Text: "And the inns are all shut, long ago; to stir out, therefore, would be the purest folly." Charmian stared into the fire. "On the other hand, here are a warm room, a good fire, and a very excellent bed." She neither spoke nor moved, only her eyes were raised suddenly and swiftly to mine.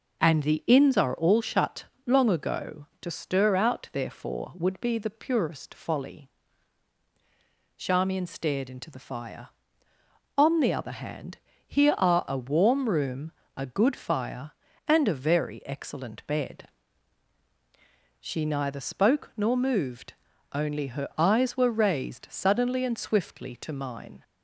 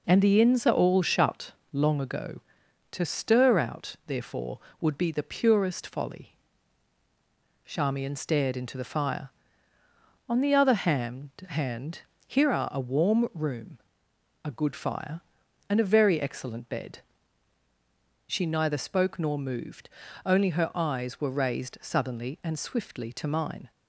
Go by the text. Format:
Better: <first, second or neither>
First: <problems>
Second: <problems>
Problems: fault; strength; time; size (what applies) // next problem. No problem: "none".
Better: first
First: none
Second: says "hand" twice; at 11.4 s